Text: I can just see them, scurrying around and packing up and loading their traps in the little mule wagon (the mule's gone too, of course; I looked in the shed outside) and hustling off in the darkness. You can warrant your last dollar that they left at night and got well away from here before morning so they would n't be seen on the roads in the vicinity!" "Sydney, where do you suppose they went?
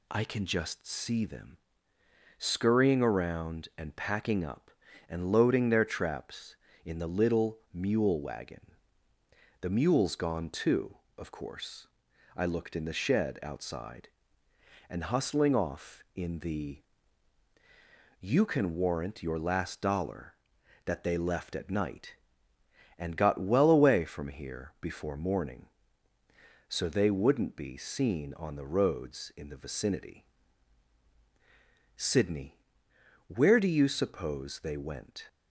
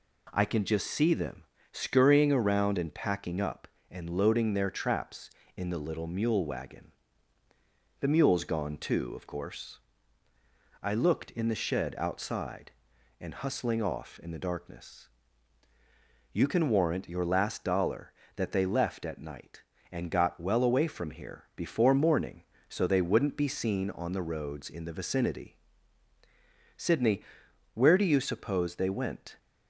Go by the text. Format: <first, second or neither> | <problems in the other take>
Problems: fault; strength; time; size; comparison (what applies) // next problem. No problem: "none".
second | pauses between "little" and "mule"; slight; at 7.5 s; 0.16 s long // skips "darkness"; at 17.5 s